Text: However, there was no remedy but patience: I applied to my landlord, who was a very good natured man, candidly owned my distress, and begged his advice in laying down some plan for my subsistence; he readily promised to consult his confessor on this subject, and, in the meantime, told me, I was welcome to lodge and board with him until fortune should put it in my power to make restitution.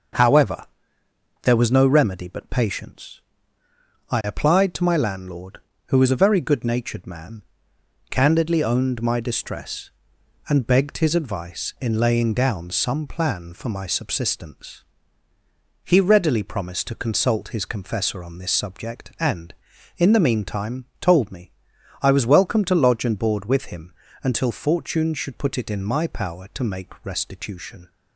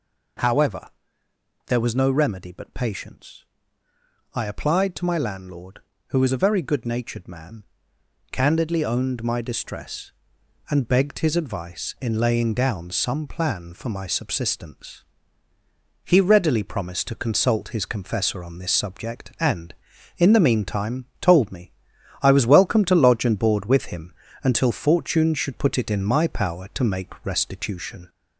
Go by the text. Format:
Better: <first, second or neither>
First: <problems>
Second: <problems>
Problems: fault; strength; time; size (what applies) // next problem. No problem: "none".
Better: first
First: pauses between "him" and "until"; slight; at 23.9 s; 0.30 s long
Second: gets louder; slight; throughout; 2 dB // pauses between "him" and "until"; slight; at 24.1 s; 0.30 s long